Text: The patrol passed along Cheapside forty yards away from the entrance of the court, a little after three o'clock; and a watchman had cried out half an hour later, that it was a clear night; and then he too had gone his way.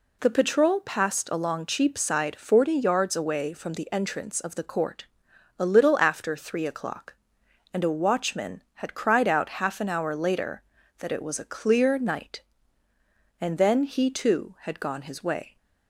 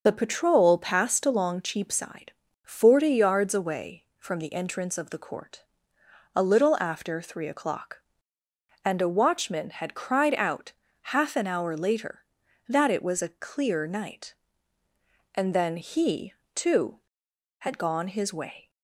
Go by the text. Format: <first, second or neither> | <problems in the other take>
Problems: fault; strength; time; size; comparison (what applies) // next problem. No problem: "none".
first | loses the start of "The"; at 0.0 s; 30 ms // starts louder than the rest; noticeable; until 1.0 s; 6 dB // pauses between "Cheapside" and "forty"; slight; at 2.3 s; 0.32 s long // pauses between "out" and "half"; at 10.7 s; 0.42 s long // pauses between "he" and "too"; slight; at 16.3 s; 0.22 s long